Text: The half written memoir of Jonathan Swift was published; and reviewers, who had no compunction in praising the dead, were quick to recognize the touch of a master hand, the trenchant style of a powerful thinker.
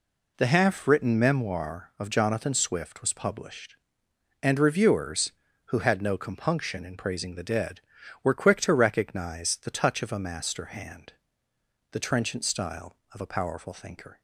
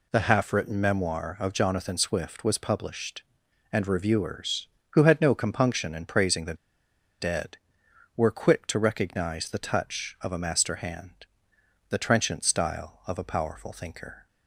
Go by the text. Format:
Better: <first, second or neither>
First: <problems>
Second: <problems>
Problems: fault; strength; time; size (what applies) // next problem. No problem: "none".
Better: first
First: none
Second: pauses between "the" and "dead"; noticeable; at 6.5 s; 0.65 s long